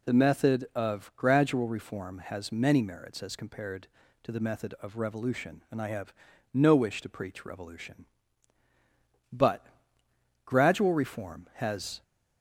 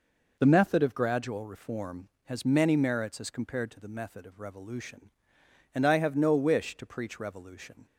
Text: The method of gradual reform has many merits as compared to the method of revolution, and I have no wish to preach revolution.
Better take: second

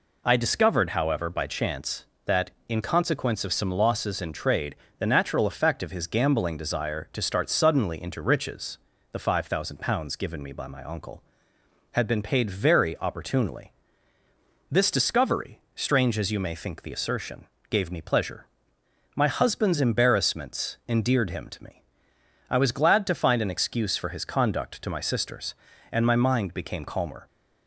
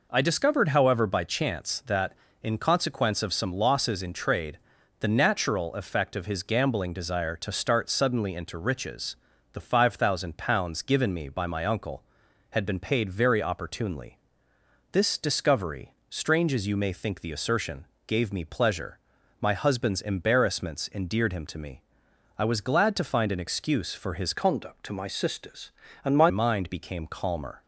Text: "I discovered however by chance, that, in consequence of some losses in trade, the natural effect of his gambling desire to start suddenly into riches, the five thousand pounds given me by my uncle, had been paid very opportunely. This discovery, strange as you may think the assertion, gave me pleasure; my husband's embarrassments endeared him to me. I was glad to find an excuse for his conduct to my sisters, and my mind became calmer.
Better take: first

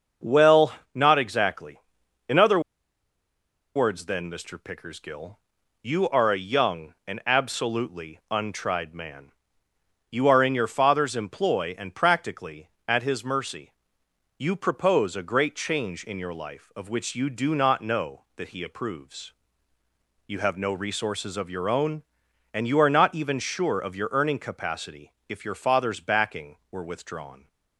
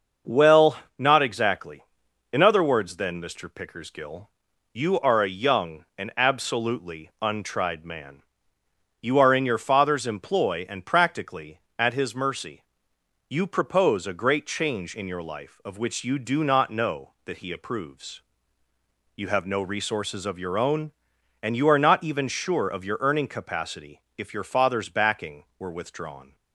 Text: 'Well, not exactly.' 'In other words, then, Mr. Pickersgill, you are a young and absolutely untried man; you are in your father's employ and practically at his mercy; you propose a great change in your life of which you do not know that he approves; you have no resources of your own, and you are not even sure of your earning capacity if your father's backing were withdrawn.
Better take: second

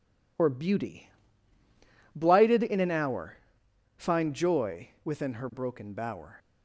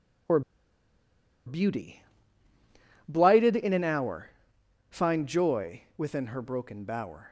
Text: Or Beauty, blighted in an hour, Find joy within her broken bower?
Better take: first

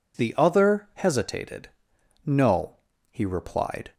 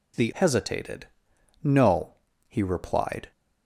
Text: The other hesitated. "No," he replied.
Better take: first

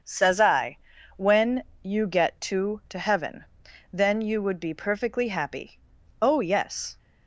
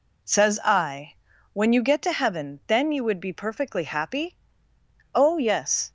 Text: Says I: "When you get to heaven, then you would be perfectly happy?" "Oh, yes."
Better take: second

